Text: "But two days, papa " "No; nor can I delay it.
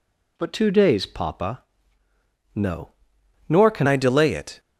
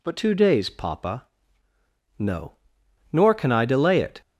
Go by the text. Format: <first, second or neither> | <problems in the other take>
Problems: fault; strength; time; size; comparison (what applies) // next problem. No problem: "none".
second | changes voice at "I"; from 3.8 s on; 0.7 s long